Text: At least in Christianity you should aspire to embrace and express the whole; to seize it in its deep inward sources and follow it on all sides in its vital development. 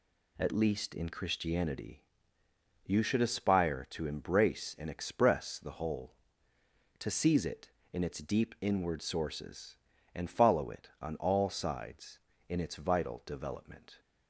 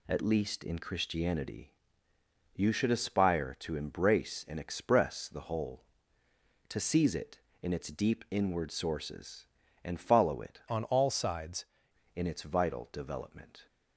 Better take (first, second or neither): first